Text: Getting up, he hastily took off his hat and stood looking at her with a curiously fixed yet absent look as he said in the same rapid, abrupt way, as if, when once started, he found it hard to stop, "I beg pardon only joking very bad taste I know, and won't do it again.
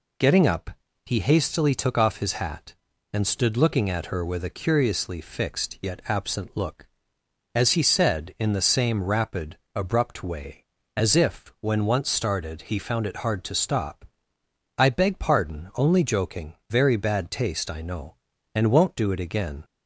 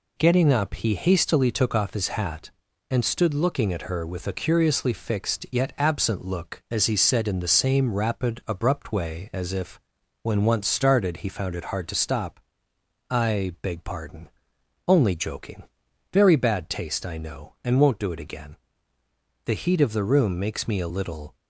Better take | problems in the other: first | pauses between "pardon" and "only"; noticeable; at 14.2 s; 0.58 s long // pauses between "joking" and "very"; noticeable; at 15.6 s; 0.48 s long // goes on to say "The heat of the room makes me a little"; strong; from 19.4 s on; 1.9 s long

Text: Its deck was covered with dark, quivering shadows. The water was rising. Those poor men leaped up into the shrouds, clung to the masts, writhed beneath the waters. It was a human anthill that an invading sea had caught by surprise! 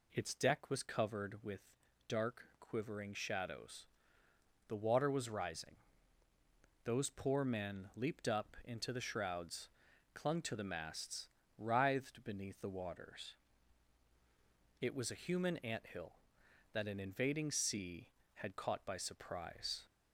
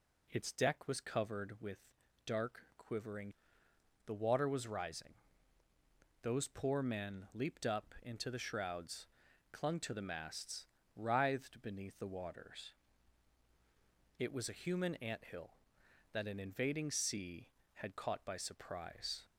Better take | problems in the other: first | pauses between "with" and "dark"; noticeable; at 1.7 s; 0.48 s long; noticeable in the first // skips "shadows"; at 3.6 s

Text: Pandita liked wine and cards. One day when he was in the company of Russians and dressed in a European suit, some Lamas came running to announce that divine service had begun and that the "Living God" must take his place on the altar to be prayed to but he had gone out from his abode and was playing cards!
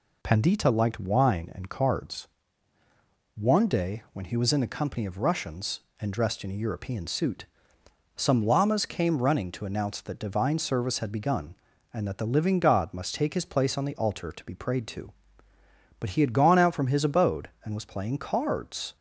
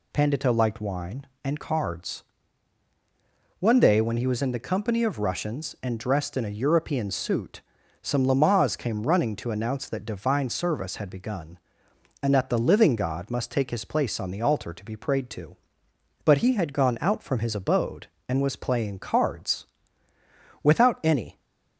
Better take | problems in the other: first | goes on to say "Without any"; noticeable; from 20.6 s on; 0.78 s long

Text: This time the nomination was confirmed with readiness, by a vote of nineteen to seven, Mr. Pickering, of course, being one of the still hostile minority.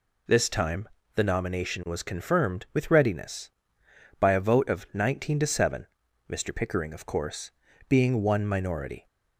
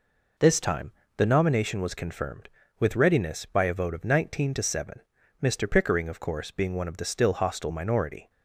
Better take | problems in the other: second | pauses between "time" and "the"; slight; at 0.8 s; 0.28 s long; slight in the second // skips "of the still hostile"; at 8.4 s

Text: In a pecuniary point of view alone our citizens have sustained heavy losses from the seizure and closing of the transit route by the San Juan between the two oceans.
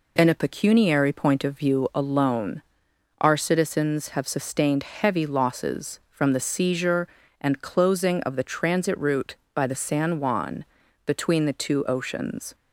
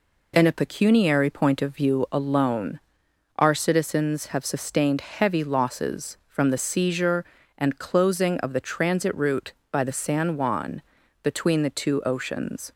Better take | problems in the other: neither | pauses between "alone" and "our"; noticeable; the same in both // pauses between "Juan" and "between"; the same in both

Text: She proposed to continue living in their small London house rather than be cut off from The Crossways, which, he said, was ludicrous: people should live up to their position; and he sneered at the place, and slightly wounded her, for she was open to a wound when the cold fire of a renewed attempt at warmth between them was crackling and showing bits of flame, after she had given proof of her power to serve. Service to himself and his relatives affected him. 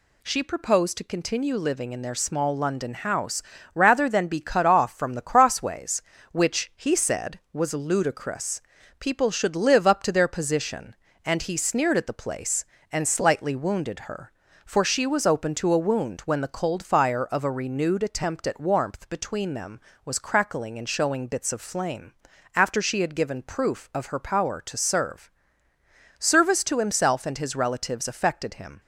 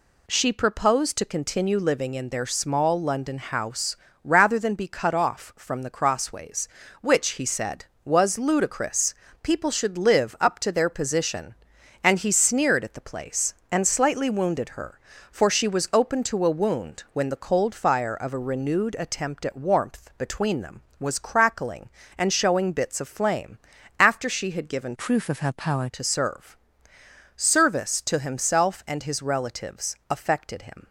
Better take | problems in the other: first | pauses between "house" and "rather"; slight; at 3.9 s; 0.28 s long; slight in the first // changes voice from "proof" to "power"; from 24.9 to 25.8 s; 0.9 s long // pauses between "relatives" and "affected"; slight; at 29.9 s; 0.16 s long

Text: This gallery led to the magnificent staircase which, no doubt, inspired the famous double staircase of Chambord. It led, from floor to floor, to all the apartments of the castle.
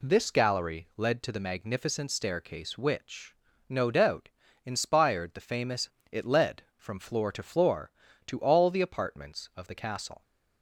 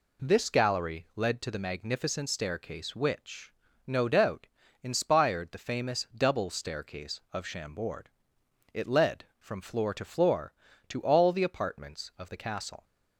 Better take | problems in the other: second | skips "double staircase of Chambord"; at 6.0 s

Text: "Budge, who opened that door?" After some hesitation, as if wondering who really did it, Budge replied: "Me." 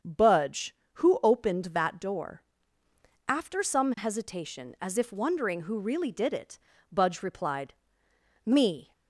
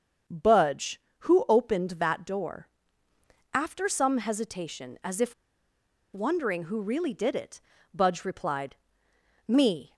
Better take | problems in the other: first | starts louder than the rest; until 1.5 s; 6.5 dB; also in the first // pauses between "if" and "wondering"; noticeable; at 5.3 s; 0.80 s long

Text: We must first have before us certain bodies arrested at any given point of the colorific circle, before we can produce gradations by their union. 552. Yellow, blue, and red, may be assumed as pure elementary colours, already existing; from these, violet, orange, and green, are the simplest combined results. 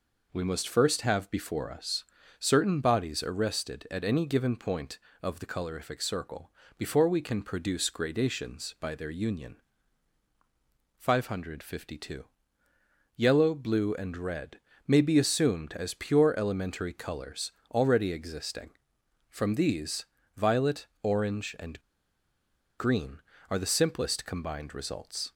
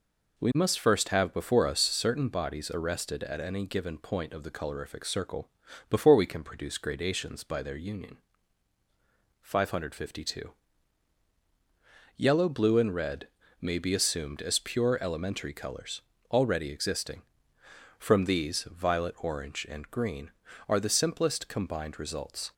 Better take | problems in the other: second | pauses between "us" and "certain"; slight; at 2.0 s; 0.34 s long // pauses between "and" and "green"; at 21.7 s; 0.98 s long

